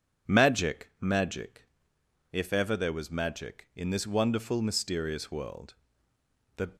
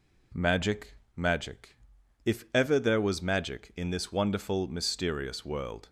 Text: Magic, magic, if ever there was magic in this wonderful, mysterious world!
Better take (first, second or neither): second